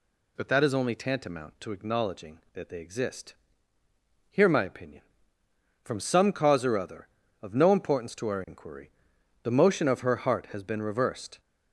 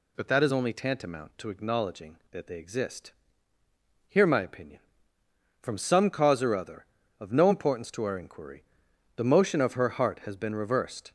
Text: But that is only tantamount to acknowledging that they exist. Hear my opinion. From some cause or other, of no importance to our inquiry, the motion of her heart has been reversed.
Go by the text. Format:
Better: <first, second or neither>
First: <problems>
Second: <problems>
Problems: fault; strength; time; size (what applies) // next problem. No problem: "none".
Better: neither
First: none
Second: none